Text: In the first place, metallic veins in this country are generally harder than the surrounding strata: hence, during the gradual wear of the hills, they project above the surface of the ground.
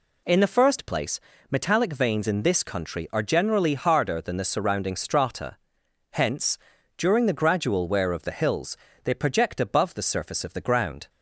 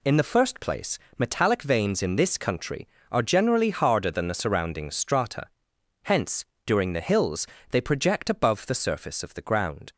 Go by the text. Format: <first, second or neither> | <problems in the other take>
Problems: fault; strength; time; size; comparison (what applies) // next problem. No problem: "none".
first | skips "gradual wear of the"; at 7.0 s